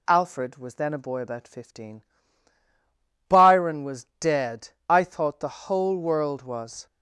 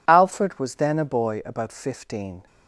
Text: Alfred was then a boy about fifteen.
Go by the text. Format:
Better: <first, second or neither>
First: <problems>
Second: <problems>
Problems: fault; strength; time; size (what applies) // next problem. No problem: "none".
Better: second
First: goes on to say "Byron was dead I thought the whole world was"; strong; from 3.2 s on; 3.5 s long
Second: none